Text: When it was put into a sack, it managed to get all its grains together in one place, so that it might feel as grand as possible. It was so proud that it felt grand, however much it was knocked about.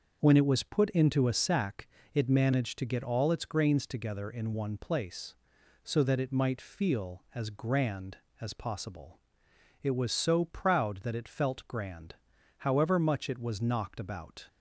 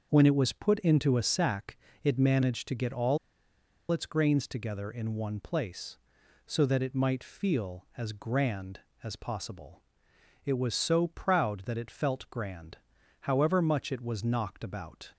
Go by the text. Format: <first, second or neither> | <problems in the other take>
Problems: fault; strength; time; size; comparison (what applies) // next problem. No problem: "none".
first | starts louder than the rest; noticeable; until 1.1 s; 6 dB; noticeable in the first // pauses between "all" and "its"; noticeable; at 3.1 s; 0.73 s long